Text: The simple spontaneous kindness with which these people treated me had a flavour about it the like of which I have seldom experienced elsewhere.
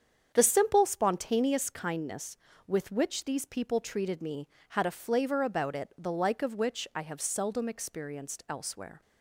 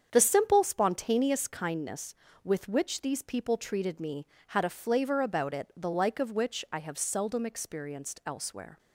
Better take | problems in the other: neither | starts louder than the rest; strong; the same in both

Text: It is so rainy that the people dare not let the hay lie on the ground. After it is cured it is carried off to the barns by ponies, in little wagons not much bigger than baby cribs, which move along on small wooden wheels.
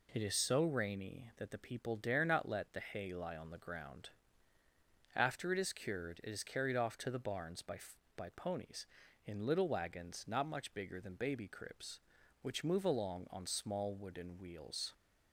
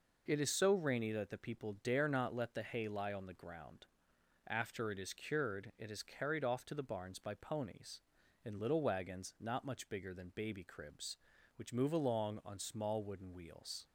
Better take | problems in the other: second | says "by" twice; at 8.1 s

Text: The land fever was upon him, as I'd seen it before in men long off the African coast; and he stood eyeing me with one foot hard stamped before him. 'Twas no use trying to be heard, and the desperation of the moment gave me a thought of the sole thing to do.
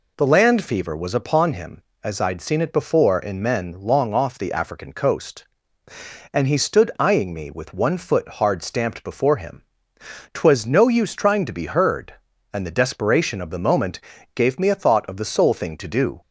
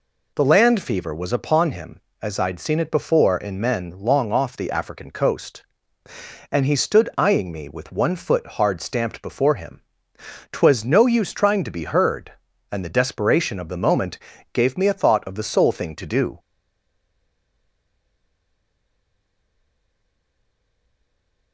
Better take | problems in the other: first | pauses between "moment" and "gave"; slight; at 14.1 s; 0.34 s long; slight in the first // stays silent after the last word; strong; from 16.3 s on; 5.2 s long

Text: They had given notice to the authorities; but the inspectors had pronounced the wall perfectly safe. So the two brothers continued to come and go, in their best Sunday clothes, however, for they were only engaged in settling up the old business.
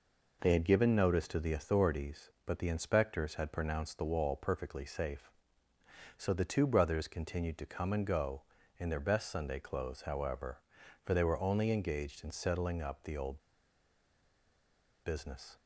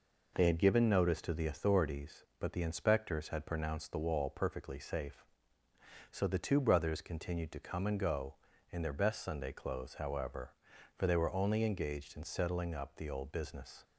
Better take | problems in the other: second | pauses between "old" and "business"; strong; at 13.3 s; 1.6 s long

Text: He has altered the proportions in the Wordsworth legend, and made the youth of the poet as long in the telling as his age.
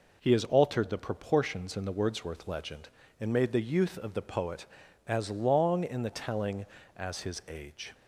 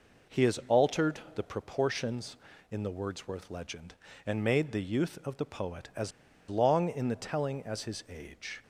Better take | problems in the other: first | pauses between "as" and "long"; at 6.1 s; 0.38 s long

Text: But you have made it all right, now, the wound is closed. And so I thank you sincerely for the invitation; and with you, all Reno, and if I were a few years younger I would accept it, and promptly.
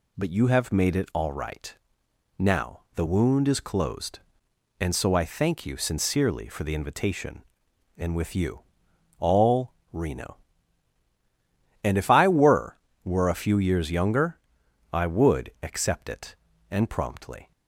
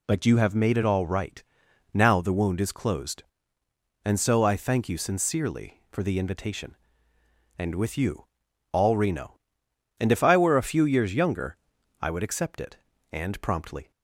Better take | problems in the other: second | pauses between "all" and "Reno"; slight; at 9.7 s; 0.20 s long // says "were" twice; at 13.0 s // pauses between "younger" and "I"; noticeable; at 14.3 s; 0.54 s long; also in the second

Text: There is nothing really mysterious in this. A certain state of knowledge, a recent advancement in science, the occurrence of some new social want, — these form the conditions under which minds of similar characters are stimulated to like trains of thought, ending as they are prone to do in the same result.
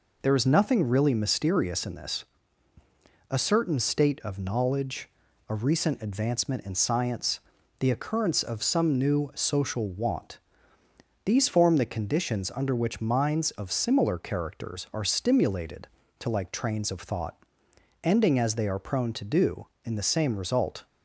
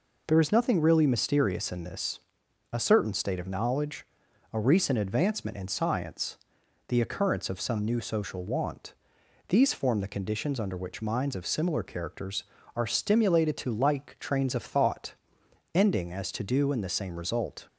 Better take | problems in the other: first | skips "they are prone"; at 16.3 s

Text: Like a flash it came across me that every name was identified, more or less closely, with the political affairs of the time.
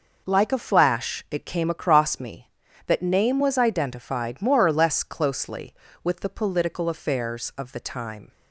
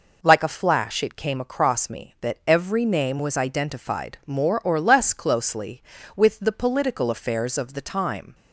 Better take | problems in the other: second | skips "every"; at 3.0 s

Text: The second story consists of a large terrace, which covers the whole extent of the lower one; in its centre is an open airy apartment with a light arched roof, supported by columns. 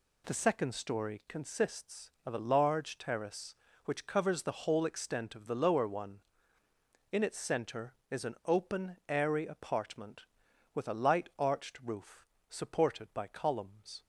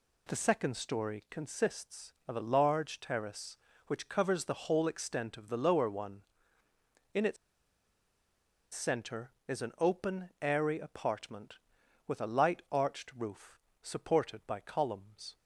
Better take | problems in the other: first | pauses between "its" and "centre"; strong; at 7.3 s; 1.3 s long

